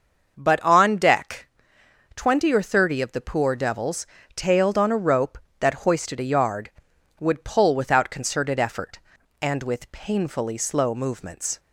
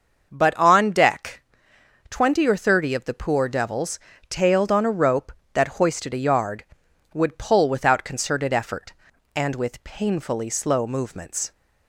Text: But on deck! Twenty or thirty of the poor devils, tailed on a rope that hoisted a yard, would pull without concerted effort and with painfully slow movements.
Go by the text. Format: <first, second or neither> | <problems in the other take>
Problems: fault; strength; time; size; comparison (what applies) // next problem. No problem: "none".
neither | starts louder than the rest; the same in both